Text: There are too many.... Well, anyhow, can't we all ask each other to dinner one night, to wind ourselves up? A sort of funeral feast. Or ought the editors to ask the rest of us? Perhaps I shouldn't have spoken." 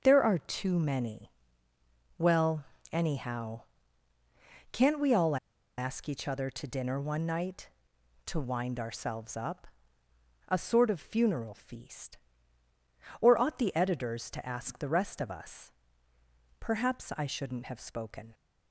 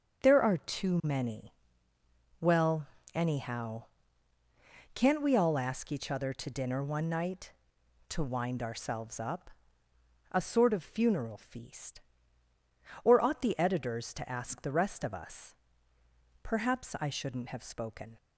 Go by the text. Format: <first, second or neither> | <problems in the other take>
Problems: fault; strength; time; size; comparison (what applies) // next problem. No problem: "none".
second | starts louder than the rest; strong; until 1.0 s; 7 dB; strong in the second // pauses between "all" and "ask"; at 5.3 s; 0.41 s long